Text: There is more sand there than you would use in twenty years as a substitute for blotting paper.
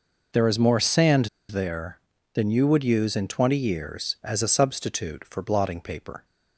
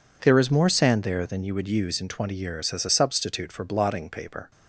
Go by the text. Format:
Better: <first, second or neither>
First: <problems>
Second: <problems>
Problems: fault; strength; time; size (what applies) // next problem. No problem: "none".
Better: second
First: pauses between "sand" and "there"; slight; at 1.2 s; 0.22 s long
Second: none